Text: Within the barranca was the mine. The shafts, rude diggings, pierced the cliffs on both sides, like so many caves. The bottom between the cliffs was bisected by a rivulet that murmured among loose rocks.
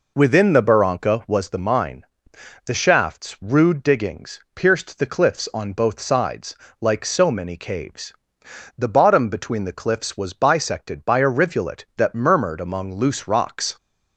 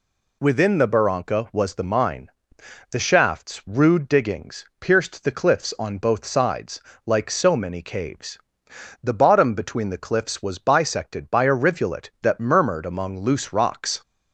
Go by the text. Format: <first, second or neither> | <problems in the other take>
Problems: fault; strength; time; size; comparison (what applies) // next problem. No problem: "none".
second | starts louder than the rest; noticeable; until 1.4 s; 4 dB